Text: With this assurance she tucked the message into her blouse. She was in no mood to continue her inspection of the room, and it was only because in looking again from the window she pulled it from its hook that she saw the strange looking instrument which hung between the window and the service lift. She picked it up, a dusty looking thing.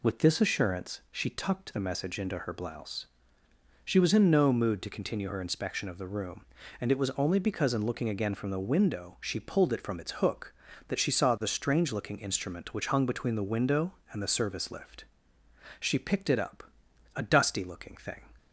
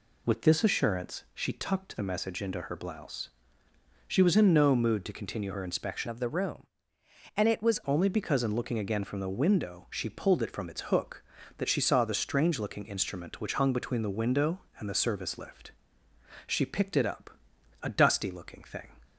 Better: first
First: none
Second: changes voice from "of" to "was"; from 6.0 to 7.8 s; 1.8 s long

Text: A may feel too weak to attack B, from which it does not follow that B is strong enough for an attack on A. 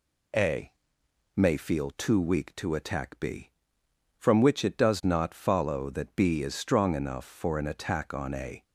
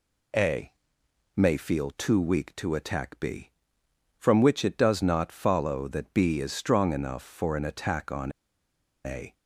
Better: first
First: pauses between "A" and "may"; noticeable; at 0.7 s; 0.62 s long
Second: pauses between "A" and "may"; noticeable; at 0.7 s; 0.62 s long // pauses between "on" and "A"; noticeable; at 8.3 s; 0.73 s long

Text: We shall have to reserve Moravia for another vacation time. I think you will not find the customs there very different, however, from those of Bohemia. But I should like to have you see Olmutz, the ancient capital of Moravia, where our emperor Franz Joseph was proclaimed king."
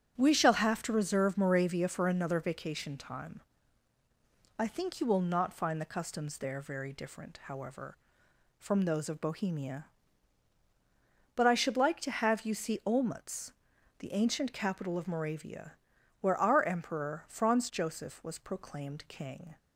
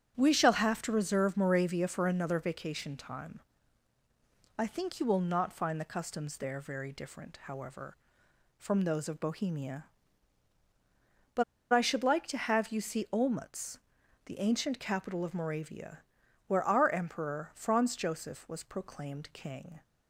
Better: first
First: starts louder than the rest; strong; until 1.2 s; 7.5 dB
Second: starts louder than the rest; strong; until 1.1 s; 8 dB // pauses between "But" and "I"; slight; at 11.4 s; 0.30 s long

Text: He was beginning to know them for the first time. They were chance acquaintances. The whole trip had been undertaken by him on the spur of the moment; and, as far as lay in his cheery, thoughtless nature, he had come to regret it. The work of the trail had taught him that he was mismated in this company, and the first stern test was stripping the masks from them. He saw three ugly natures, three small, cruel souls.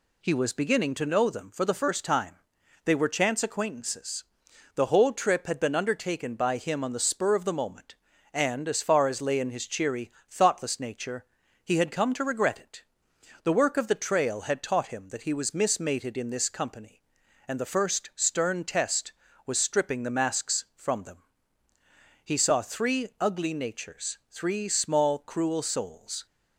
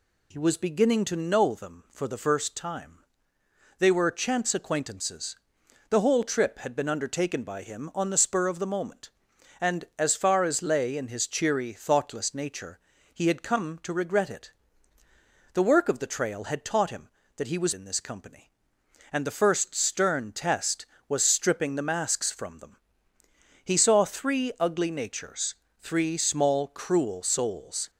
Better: first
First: none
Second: skips "mismated"; at 17.7 s

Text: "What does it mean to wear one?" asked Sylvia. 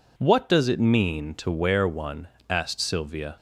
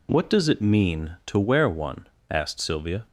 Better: neither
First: none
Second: none

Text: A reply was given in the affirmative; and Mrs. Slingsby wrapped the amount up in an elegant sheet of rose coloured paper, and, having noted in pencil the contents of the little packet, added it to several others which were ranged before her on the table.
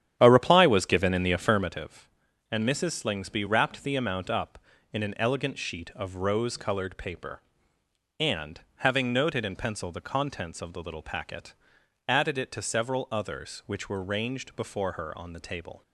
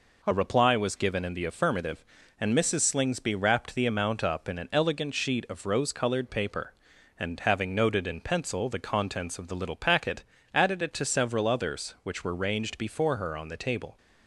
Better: second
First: starts louder than the rest; strong; until 1.7 s; 10 dB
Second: none

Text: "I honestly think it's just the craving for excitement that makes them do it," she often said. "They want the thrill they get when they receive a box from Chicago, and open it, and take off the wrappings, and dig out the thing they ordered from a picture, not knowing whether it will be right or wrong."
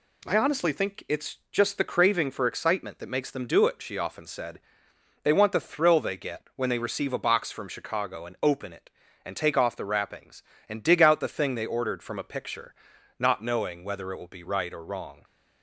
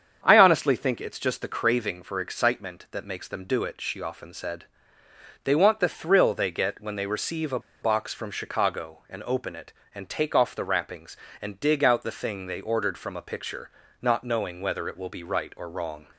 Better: first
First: none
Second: starts louder than the rest; strong; until 1.2 s; 7.5 dB // pauses between "a" and "box"; slight; at 7.5 s; 0.22 s long

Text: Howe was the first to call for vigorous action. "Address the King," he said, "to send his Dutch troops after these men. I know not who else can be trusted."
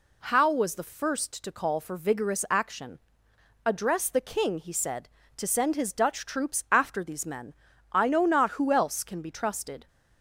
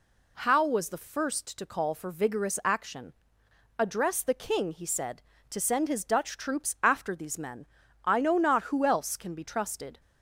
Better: neither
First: none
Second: none

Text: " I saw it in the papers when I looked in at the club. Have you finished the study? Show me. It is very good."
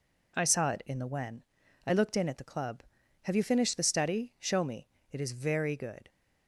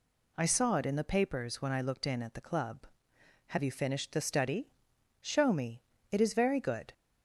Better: second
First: skips "papers"; at 1.0 s // pauses between "when" and "I"; at 1.4 s; 0.42 s long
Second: none

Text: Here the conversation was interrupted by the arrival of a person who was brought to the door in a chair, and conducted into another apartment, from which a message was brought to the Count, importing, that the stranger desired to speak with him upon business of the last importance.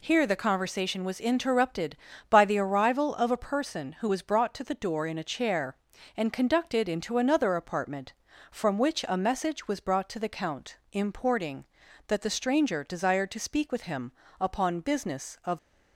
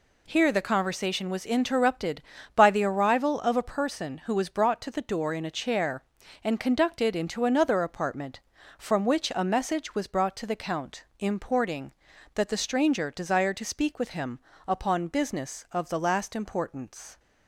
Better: second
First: pauses between "him" and "upon"; slight; at 14.1 s; 0.28 s long // stops before "the last importance"; at 15.5 s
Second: pauses between "him" and "upon"; slight; at 14.3 s; 0.28 s long

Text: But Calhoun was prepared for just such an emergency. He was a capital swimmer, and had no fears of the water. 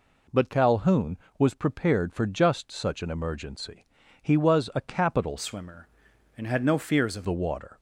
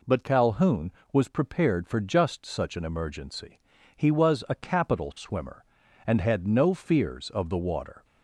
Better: second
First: changes voice from "swimmer" to "of"; from 5.3 to 7.2 s; 1.9 s long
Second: none

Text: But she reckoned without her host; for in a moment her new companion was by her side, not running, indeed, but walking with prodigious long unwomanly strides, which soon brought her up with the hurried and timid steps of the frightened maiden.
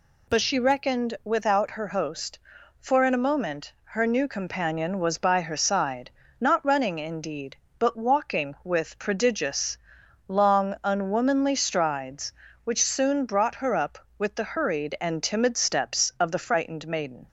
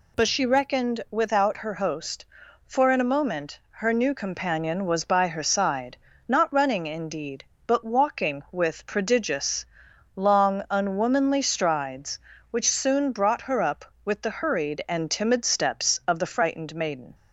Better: neither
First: pauses between "prodigious" and "long"; noticeable; at 9.7 s; 0.48 s long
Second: pauses between "prodigious" and "long"; noticeable; at 9.6 s; 0.48 s long

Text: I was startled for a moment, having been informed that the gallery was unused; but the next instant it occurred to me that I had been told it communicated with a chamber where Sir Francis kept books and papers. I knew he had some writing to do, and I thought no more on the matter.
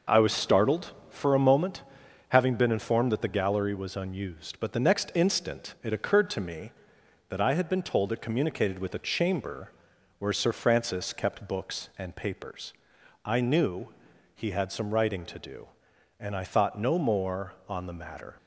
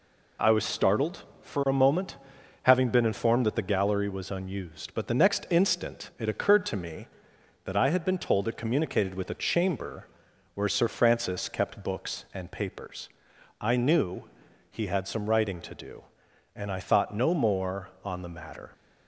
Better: second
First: starts louder than the rest; noticeable; until 1.6 s; 5.5 dB // pauses between "chamber" and "where"; noticeable; at 9.7 s; 0.46 s long // pauses between "knew" and "he"; at 13.8 s; 0.44 s long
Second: pauses between "chamber" and "where"; noticeable; at 10.0 s; 0.46 s long // pauses between "knew" and "he"; at 14.2 s; 0.44 s long

